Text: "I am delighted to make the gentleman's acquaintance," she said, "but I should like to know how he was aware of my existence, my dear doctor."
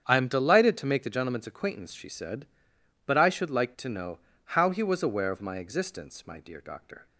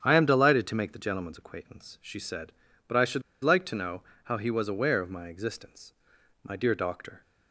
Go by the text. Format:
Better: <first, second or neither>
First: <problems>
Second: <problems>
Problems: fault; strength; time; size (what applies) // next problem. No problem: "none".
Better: first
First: starts louder than the rest; strong; until 1.0 s; 8.5 dB // pauses between "know" and "how"; slight; at 4.1 s; 0.28 s long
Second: starts louder than the rest; strong; until 1.0 s; 9 dB // pauses between "should" and "like"; slight; at 3.2 s; 0.21 s long // pauses between "know" and "how"; slight; at 4.0 s; 0.22 s long